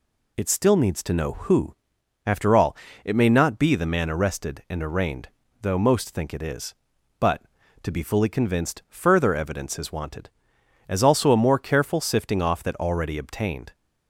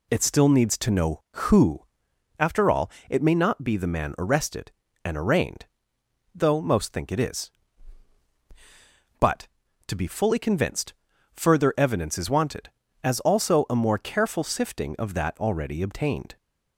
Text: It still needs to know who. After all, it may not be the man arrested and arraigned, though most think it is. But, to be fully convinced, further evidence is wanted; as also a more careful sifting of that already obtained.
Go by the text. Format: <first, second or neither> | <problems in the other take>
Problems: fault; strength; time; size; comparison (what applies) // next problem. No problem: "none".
second | says "off" for "of"; at 12.4 s